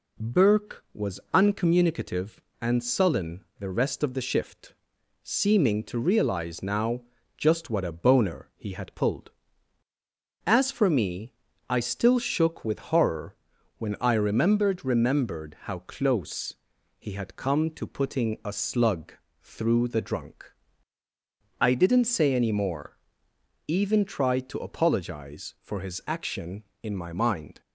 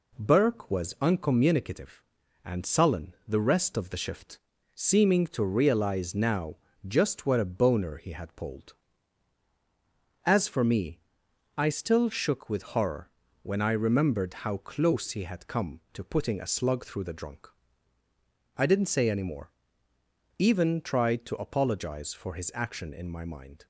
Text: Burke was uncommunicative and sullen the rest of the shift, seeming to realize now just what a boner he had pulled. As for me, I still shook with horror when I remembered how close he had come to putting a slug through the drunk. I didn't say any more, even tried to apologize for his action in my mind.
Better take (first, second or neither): second